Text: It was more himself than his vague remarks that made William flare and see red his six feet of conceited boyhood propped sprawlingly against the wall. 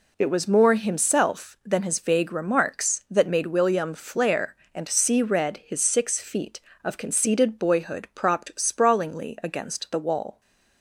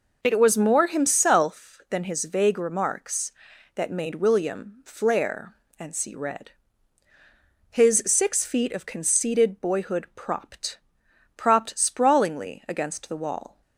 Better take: first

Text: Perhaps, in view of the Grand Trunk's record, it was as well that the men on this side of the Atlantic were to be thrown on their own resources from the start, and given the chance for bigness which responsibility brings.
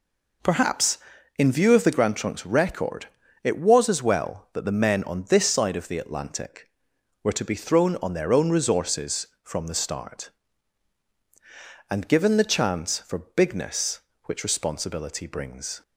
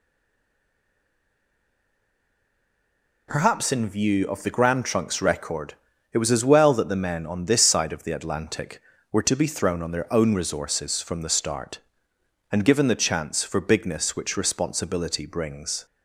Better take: first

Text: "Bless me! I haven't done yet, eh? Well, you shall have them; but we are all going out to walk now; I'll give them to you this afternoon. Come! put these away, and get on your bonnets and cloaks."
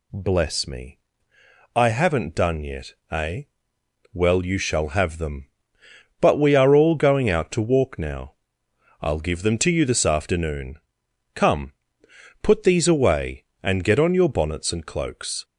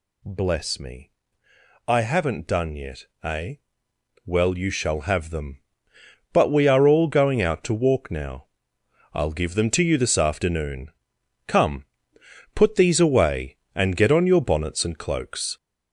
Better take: first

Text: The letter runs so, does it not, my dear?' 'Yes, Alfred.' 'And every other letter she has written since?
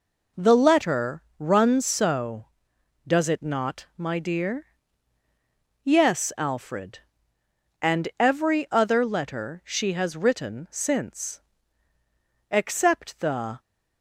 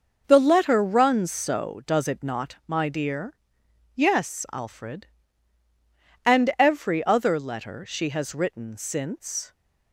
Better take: second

